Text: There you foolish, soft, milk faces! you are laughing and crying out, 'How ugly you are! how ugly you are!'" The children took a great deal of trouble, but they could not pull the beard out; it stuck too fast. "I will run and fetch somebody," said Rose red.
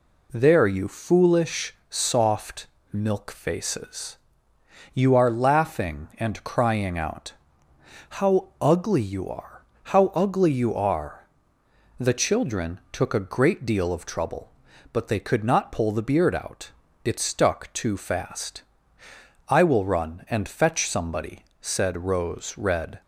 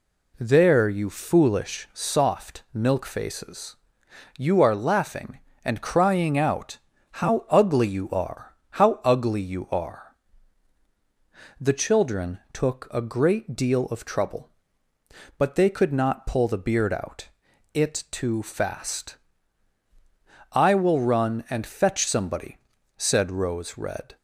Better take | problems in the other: first | skips "stuck"; at 18.0 s

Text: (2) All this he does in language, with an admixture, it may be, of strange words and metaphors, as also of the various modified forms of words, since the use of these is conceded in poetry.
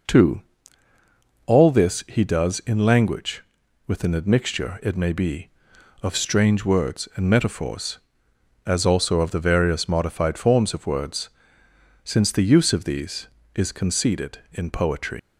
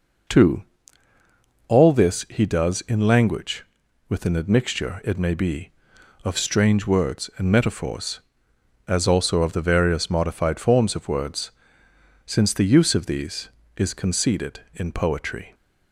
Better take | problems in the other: second | leaves "poetry" unfinished; at 15.1 s; 125 ms

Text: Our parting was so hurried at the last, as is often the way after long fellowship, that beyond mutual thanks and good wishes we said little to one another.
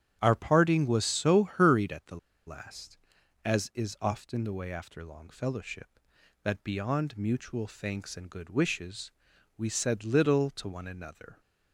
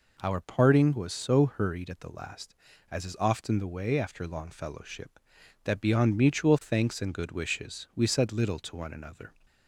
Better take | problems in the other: second | starts louder than the rest; strong; until 1.2 s; 9.5 dB // pauses between "the" and "last"; slight; at 2.1 s; 0.29 s long // pauses between "wishes" and "we"; noticeable; at 9.0 s; 0.48 s long

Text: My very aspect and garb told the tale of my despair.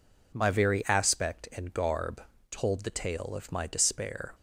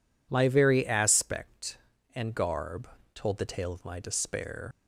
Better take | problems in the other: first | pauses between "garb" and "told"; slight; at 2.8 s; 0.28 s long; slight in the first // leaves "despair" unfinished; at 4.7 s; 95 ms

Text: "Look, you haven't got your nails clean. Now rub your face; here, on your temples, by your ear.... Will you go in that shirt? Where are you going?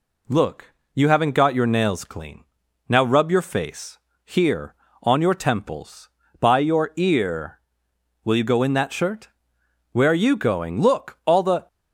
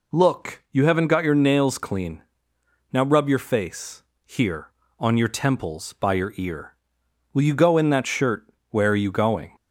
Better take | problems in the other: second | goes on to say "Look all the"; noticeable; from 10.8 s on; 0.86 s long

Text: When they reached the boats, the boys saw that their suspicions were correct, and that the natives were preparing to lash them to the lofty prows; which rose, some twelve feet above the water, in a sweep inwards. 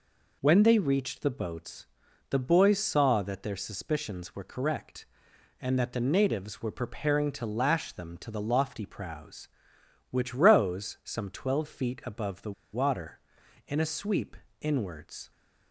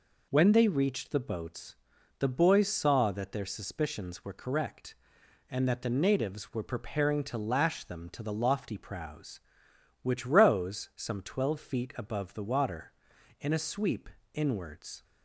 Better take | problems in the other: second | pauses between "the" and "water"; slight; at 12.5 s; 0.20 s long // pauses between "sweep" and "inwards"; slight; at 14.3 s; 0.24 s long; slight in the second

